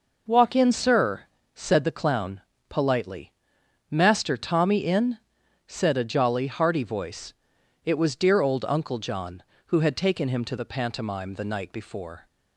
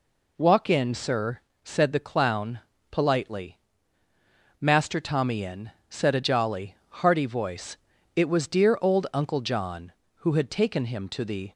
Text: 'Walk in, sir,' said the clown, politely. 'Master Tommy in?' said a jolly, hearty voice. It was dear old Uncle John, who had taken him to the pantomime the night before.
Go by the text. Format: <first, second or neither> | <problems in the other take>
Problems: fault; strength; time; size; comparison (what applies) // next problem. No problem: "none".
first | stops before "pantomime the night before"; at 11.5 s